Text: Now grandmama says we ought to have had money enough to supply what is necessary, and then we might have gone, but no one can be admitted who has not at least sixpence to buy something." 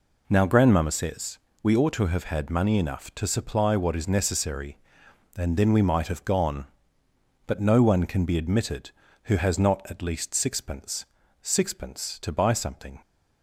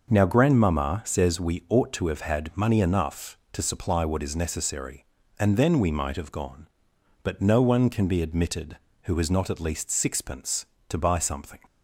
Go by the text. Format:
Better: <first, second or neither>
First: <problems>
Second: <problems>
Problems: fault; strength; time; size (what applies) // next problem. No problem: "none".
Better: second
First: pauses between "says" and "we"; slight; at 1.3 s; 0.24 s long // says "sixpence" twice; at 11.4 s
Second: none